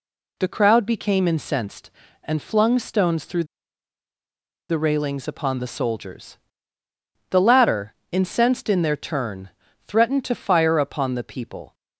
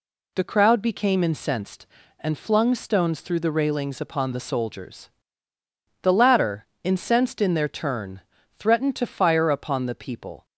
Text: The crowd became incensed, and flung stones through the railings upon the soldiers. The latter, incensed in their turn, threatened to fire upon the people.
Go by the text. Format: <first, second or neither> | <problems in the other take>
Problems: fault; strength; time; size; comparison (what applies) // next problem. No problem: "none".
second | pauses between "through" and "the"; at 3.4 s; 1.2 s long